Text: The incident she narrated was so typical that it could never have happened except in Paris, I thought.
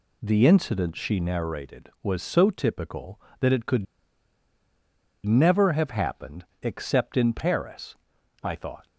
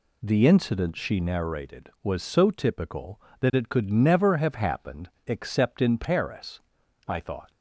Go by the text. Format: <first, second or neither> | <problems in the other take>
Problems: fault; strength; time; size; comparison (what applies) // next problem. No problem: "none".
second | pauses between "could" and "never"; strong; at 3.8 s; 1.4 s long // pauses between "happened" and "except"; slight; at 6.4 s; 0.16 s long; slight in the second